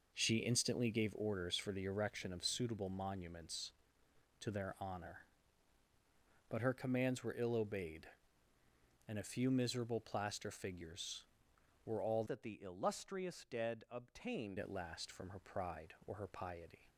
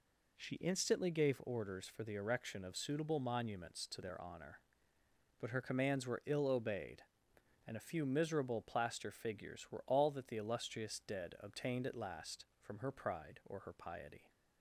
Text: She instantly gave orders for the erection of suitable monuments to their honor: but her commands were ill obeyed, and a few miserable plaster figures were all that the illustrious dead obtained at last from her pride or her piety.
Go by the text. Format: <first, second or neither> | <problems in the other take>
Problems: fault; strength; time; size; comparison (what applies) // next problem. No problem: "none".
second | changes voice from "that" to "obtained"; from 12.2 to 14.5 s; 2.3 s long